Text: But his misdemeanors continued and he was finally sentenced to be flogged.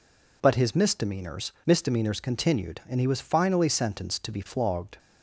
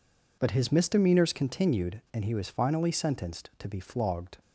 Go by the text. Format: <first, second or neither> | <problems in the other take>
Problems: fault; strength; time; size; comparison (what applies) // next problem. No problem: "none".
second | says "misdemeanors" twice; at 1.6 s